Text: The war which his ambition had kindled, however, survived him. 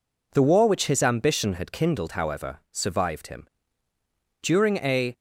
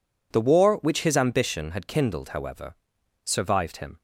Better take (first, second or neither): second